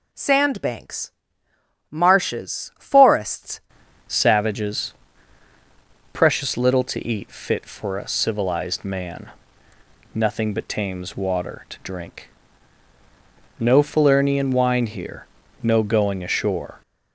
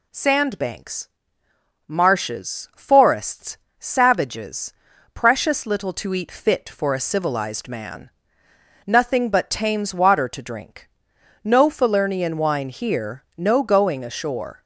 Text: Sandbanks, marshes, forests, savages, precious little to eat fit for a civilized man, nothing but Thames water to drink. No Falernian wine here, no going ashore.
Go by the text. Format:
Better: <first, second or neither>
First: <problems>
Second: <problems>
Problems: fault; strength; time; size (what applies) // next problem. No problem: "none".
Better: second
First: changes voice at "savages"; from 4.0 s on; 12.8 s long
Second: none